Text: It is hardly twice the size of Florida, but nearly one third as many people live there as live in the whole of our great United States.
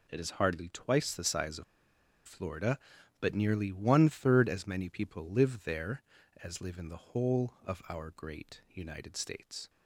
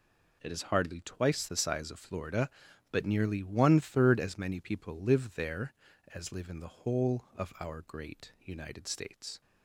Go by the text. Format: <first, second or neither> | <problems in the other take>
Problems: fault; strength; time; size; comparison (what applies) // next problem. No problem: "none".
second | pauses between "of" and "Florida"; noticeable; at 1.6 s; 0.63 s long